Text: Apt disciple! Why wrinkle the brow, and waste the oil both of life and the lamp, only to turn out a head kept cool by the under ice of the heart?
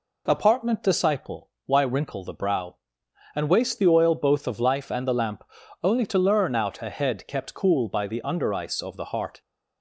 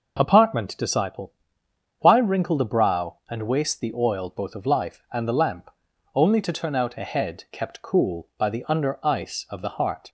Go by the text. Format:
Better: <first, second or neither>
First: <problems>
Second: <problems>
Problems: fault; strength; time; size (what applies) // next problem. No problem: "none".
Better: second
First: says "learn" for "turn"; at 6.1 s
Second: none